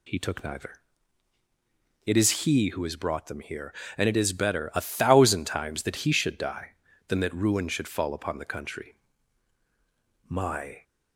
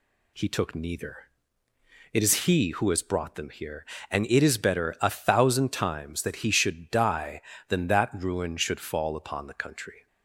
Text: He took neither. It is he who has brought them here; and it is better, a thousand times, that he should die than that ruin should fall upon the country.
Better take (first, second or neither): second